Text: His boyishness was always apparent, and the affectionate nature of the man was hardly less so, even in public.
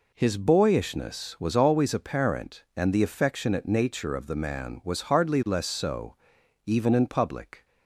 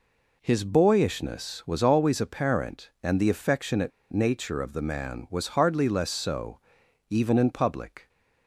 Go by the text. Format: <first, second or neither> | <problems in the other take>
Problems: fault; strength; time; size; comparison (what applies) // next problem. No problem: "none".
first | pauses between "affectionate" and "nature"; slight; at 3.9 s; 0.21 s long